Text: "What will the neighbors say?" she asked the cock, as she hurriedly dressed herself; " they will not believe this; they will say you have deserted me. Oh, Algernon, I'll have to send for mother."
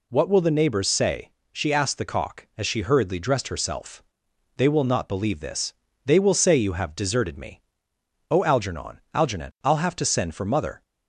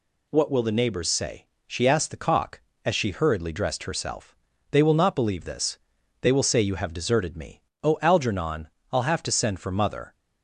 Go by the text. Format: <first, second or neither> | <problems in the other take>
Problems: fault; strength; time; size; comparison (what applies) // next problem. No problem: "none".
second | says "Algernon" twice; at 9.1 s